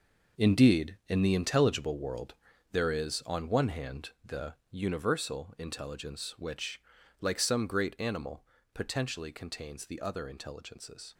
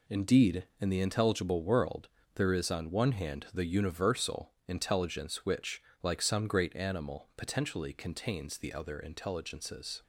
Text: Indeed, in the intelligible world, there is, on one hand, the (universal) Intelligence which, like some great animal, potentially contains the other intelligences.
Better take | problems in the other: second | gets quieter; strong; throughout; 11 dB

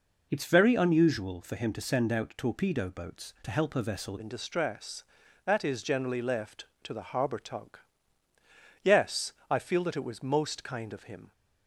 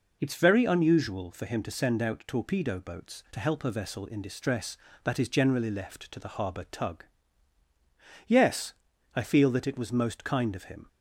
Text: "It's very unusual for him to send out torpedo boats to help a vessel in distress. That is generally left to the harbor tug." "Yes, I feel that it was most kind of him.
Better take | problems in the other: second | changes voice at "in"; from 4.1 s on; 7.2 s long

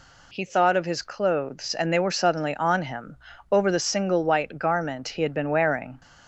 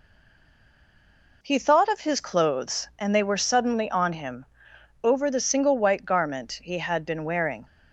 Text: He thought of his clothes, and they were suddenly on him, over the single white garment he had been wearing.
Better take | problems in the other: first | stays silent before the first word; noticeable; until 1.4 s; 1.4 s long

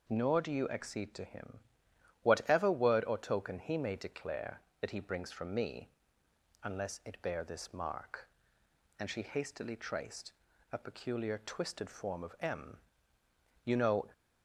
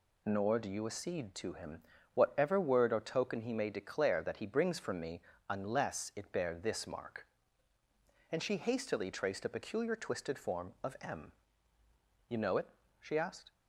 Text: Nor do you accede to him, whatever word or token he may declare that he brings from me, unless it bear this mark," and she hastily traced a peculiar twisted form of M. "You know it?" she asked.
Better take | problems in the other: second | pauses between "traced" and "a"; at 10.3 s; 0.40 s long // stops before "it she asked"; at 14.1 s

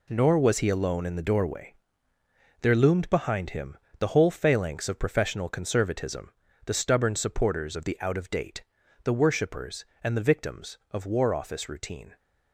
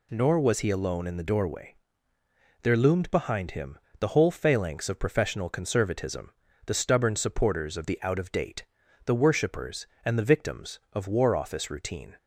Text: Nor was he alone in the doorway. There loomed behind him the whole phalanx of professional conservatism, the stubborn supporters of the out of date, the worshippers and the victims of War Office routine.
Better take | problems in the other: second | gets quieter; strong; throughout; 9.5 dB // pauses between "him" and "the"; slight; at 3.7 s; 0.22 s long; slight in the second

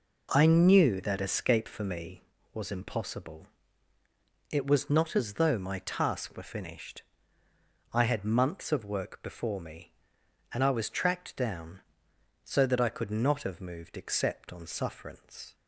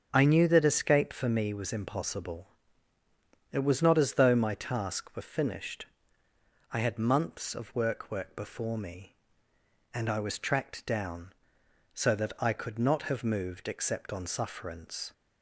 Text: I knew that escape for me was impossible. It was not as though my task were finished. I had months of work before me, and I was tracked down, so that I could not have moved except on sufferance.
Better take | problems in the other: first | starts louder than the rest; until 1.1 s; 6.5 dB // says "work" twice; at 8.1 s

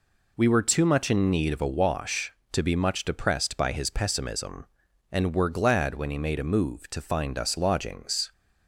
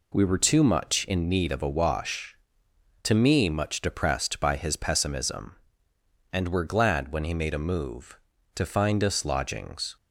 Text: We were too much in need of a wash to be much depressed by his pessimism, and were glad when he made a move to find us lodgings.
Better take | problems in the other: first | says "me" for "be"; at 3.1 s

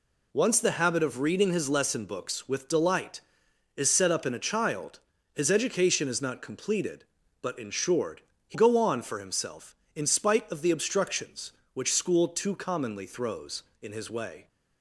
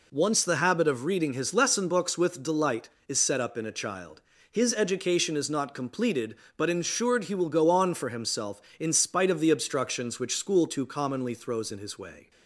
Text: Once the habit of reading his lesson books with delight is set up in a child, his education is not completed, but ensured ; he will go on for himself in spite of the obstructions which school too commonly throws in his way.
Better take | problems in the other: second | skips "will"; at 8.5 s

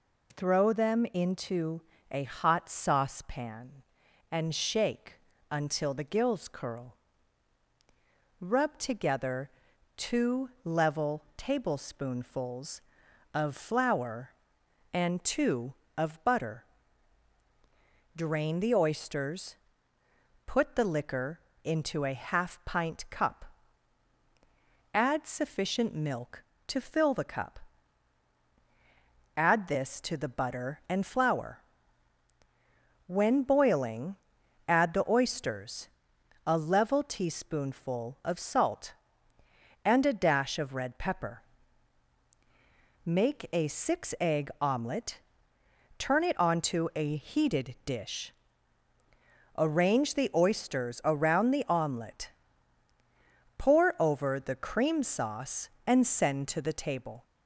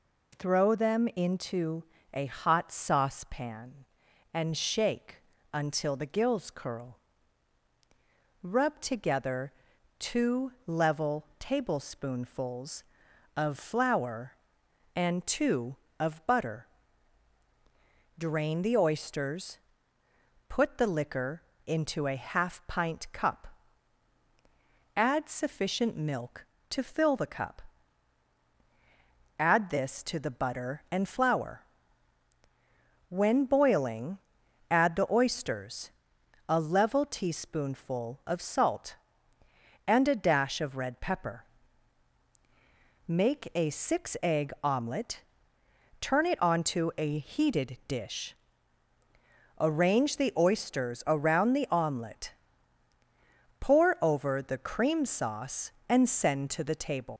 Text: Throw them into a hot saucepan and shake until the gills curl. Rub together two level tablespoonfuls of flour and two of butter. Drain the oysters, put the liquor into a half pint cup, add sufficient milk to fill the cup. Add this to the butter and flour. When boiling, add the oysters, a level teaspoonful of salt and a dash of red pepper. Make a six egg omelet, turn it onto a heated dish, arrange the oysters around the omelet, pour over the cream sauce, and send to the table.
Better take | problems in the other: first | pauses between "into" and "a"; slight; at 1.8 s; 0.28 s long; slight in the first // pauses between "shake" and "until"; slight; at 5.1 s; 0.34 s long; slight in the first // pauses between "together" and "two"; noticeable; at 9.5 s; 0.48 s long; noticeable in the first // pauses between "liquor" and "into"; slight; at 21.4 s; 0.24 s long; slight in the first // leaves "table" unfinished; at 57.1 s; 95 ms

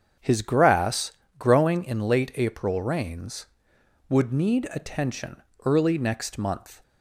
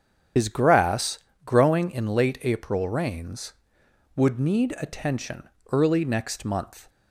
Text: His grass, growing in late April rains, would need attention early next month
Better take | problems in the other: first | loses the start of "His"; at 0.3 s; 95 ms // starts louder than the rest; strong; until 1.6 s; 8.5 dB; also in the first // pauses between "attention" and "early"; slight; at 5.4 s; 0.22 s long; slight in the first

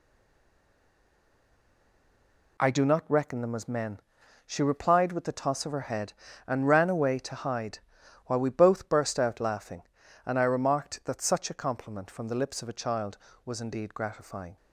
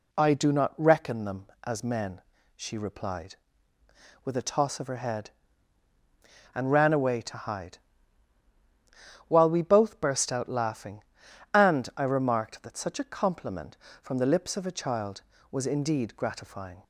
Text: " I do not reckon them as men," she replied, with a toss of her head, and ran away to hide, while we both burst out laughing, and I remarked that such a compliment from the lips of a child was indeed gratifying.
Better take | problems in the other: second | stays silent before the first word; strong; until 2.5 s; 2.5 s long

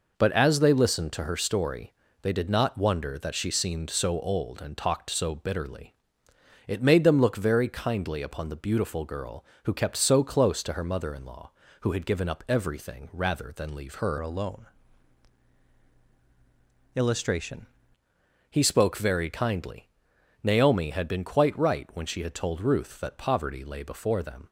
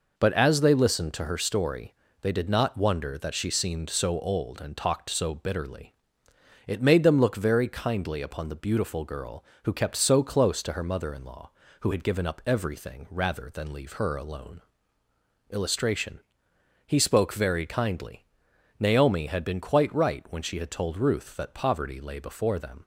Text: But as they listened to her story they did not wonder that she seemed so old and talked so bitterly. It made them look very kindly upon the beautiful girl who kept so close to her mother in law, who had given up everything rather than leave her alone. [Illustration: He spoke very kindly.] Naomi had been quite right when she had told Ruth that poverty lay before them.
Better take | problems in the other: second | pauses between "story" and "they"; slight; at 1.9 s; 0.28 s long; slight in the second // changes voice from "alone" to "Illustration"; from 14.1 to 17.6 s; 3.5 s long

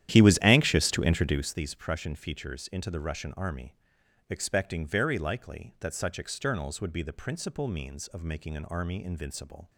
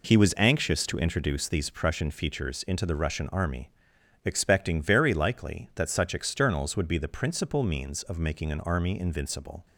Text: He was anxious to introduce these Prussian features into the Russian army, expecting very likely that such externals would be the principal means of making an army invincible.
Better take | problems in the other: second | starts louder than the rest; strong; until 1.6 s; 11.5 dB

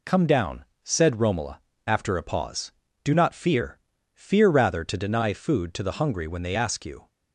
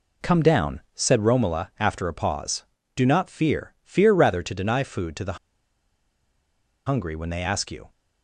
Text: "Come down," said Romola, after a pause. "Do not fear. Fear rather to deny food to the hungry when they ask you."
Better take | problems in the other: first | pauses between "the" and "hungry"; strong; at 5.3 s; 1.5 s long

